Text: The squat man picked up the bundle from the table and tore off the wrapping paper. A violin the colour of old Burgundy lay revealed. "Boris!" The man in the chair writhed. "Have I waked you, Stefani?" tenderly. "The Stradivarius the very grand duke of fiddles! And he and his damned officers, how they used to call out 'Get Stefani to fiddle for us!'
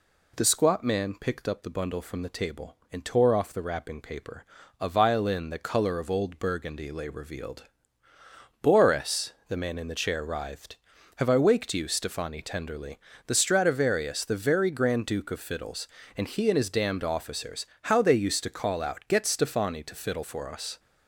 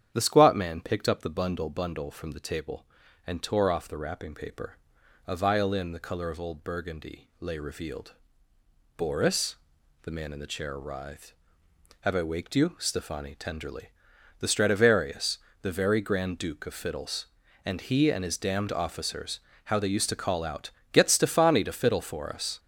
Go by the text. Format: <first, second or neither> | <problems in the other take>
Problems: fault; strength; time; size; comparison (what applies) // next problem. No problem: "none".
first | starts louder than the rest; strong; until 1.1 s; 9 dB // says "bundle" twice; at 1.6 s // pauses between "Stradivarius" and "the"; slight; at 15.3 s; 0.24 s long // pauses between "out" and "Get"; slight; at 20.6 s; 0.24 s long